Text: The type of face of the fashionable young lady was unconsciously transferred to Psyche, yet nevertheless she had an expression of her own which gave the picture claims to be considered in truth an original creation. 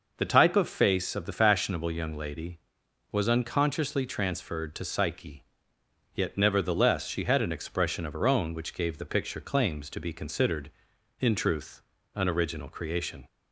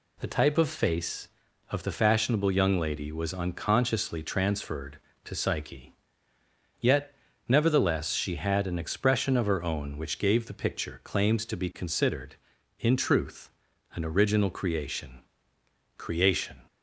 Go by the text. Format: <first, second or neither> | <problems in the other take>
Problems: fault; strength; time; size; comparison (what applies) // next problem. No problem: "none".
first | pauses between "yet" and "nevertheless"; slight; at 7.1 s; 0.34 s long // pauses between "truth" and "an"; noticeable; at 13.4 s; 0.46 s long; slight in the first // says "creation" twice; at 15.9 s